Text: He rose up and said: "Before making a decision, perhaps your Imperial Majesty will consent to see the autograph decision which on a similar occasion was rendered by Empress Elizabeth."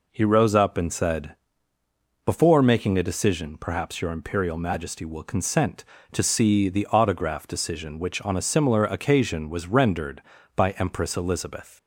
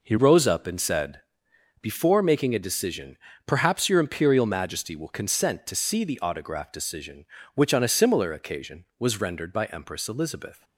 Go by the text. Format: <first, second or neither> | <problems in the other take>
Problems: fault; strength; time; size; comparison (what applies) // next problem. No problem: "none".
first | changes voice at "rose"; from 0.1 s on; 10.5 s long